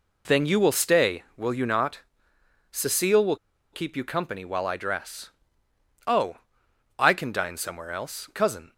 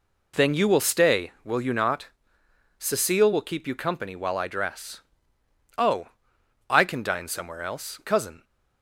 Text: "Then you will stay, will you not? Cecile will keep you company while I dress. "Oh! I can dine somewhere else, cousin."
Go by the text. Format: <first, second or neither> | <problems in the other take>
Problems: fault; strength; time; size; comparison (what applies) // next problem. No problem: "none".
second | pauses between "will" and "keep"; at 3.3 s; 0.36 s long